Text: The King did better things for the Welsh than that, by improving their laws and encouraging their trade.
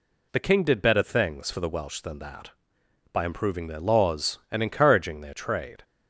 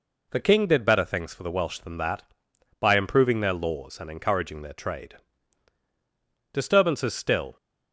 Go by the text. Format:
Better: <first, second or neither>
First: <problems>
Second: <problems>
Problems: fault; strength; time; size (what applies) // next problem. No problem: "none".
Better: first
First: none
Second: goes on to say "Disturbances still"; noticeable; from 6.5 s on; 1.0 s long